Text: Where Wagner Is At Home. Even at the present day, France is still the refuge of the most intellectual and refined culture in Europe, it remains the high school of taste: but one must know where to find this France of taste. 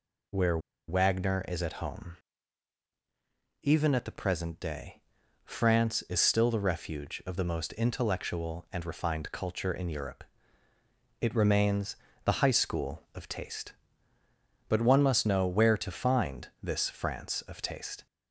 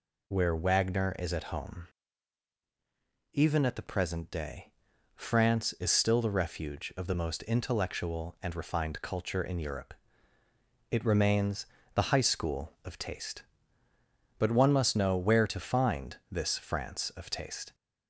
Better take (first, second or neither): second